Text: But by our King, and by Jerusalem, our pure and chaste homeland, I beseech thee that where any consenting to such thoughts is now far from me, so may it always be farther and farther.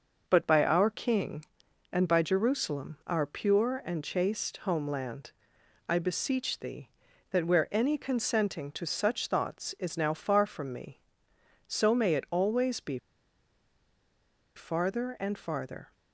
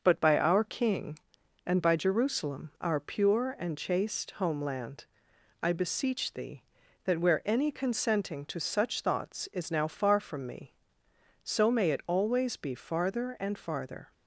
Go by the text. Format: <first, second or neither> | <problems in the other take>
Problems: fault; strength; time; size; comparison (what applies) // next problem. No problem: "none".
second | starts louder than the rest; until 1.2 s; 6 dB; also in the second // pauses between "be" and "farther"; strong; at 12.9 s; 1.5 s long